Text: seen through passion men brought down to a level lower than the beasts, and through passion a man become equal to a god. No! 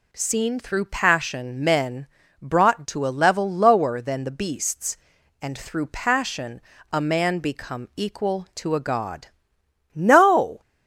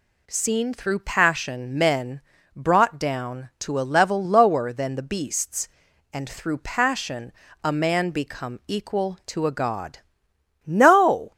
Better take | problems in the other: second | pauses between "men" and "brought"; slight; at 2.0 s; 0.34 s long; slight in the second // skips "down"; at 2.8 s // pauses between "passion" and "a"; slight; at 6.6 s; 0.30 s long; slight in the second

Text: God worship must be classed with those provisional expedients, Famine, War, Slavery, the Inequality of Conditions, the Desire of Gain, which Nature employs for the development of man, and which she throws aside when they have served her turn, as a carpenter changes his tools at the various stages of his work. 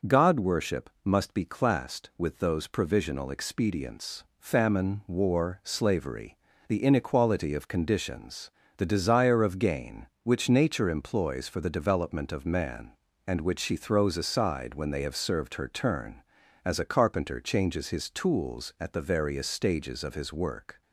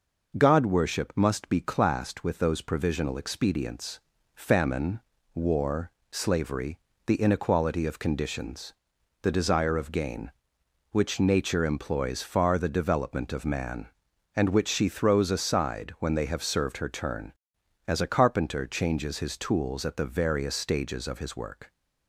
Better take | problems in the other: first | says "far" for "for"; at 12.2 s

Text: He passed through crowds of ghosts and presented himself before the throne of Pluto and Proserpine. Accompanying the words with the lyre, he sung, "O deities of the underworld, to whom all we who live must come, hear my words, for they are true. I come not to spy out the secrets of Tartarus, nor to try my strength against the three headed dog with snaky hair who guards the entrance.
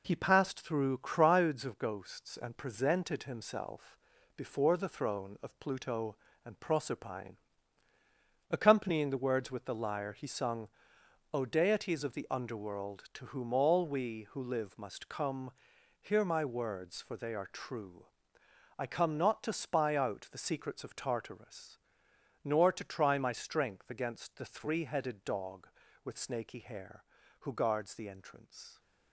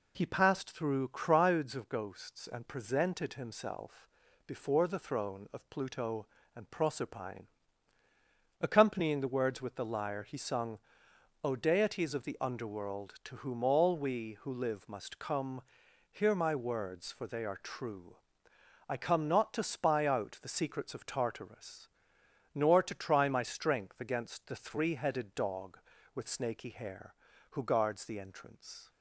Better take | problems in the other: second | gets quieter; noticeable; throughout; 5.5 dB // pauses between "himself" and "before"; at 3.9 s; 0.38 s long; also in the second

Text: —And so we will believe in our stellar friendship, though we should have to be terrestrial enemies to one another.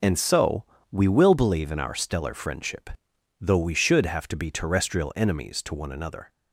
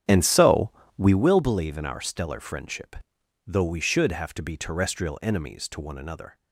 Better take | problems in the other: first | starts louder than the rest; strong; until 1.2 s; 9.5 dB // pauses between "so" and "we"; slight; at 0.7 s; 0.26 s long; slight in the first

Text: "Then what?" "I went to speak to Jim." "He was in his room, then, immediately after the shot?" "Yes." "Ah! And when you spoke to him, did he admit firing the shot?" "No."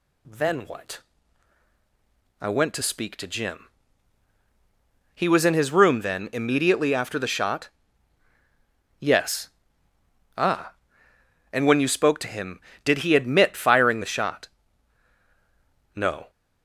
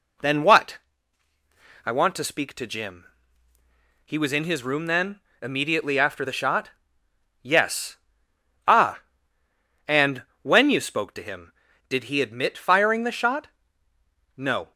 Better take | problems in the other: first | says "want" for "went"; at 1.9 s // pauses between "And" and "when"; slight; at 10.2 s; 0.22 s long

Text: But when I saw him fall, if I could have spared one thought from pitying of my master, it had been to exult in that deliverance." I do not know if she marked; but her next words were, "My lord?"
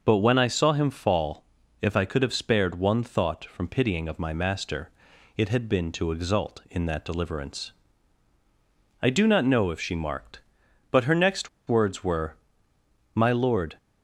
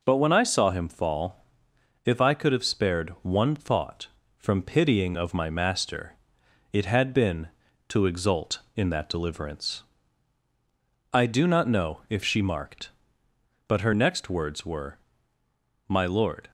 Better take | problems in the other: second | pauses between "next" and "words"; slight; at 11.4 s; 0.20 s long

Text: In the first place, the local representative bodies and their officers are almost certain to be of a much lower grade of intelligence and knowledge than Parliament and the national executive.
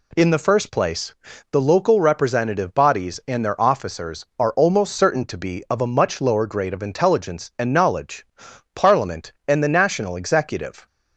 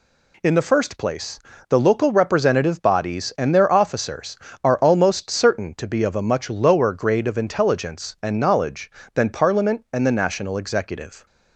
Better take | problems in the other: second | skips "than"; at 8.5 s

